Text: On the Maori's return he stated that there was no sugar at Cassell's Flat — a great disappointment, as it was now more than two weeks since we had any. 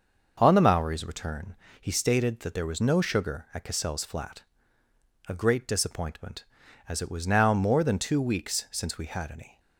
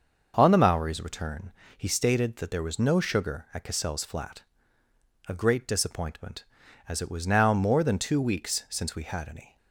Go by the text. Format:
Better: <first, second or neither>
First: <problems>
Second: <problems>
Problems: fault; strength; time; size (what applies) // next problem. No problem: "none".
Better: neither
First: starts louder than the rest; until 1.4 s; 6 dB // pauses between "return" and "he"; slight; at 1.5 s; 0.24 s long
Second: starts louder than the rest; until 1.3 s; 6.5 dB // pauses between "return" and "he"; slight; at 1.5 s; 0.24 s long